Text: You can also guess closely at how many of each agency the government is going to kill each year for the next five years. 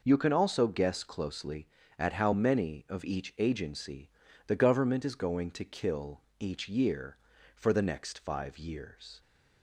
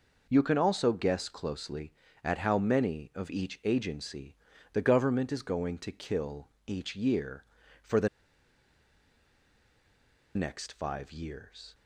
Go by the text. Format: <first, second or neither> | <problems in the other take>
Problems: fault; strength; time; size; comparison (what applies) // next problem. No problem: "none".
first | pauses between "agency" and "the"; at 4.3 s; 0.38 s long; also in the first // pauses between "kill" and "each"; slight; at 6.4 s; 0.18 s long; slight in the first // pauses between "the" and "next"; strong; at 8.0 s; 2.2 s long